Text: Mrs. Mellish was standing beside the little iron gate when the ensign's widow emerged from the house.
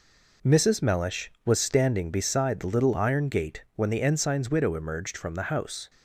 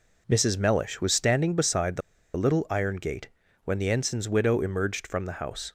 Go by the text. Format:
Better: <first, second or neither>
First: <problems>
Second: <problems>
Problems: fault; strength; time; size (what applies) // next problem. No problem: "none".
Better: first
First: none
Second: pauses between "the" and "little"; at 2.0 s; 0.36 s long // pauses between "gate" and "when"; at 3.2 s; 0.38 s long